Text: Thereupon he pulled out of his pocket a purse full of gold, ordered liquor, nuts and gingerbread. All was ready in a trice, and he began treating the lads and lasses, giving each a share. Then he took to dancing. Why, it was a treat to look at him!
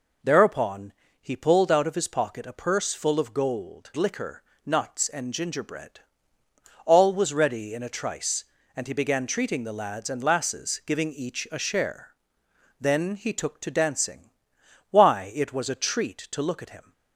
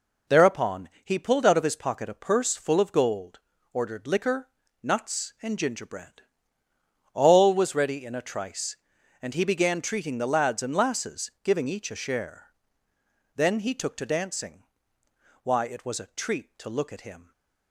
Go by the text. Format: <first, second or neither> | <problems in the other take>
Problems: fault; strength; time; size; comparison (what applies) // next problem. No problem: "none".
second | pauses between "Thereupon" and "he"; slight; at 0.9 s; 0.28 s long // skips "ordered"; at 3.9 s